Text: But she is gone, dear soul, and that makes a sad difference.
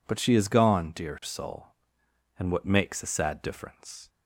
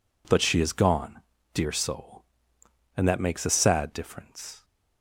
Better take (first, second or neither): second